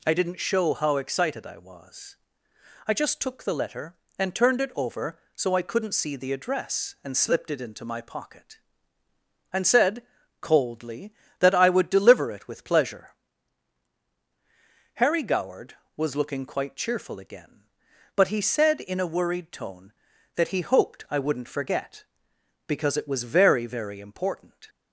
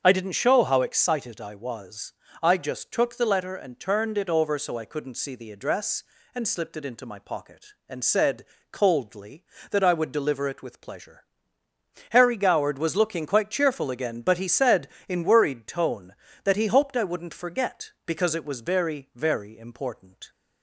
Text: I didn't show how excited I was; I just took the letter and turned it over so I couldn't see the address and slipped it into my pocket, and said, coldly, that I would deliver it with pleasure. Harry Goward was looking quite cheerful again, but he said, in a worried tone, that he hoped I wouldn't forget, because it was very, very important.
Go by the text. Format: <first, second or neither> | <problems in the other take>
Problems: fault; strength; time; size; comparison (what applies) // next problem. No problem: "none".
first | starts louder than the rest; until 1.0 s; 7 dB // skips "a"; at 15.2 s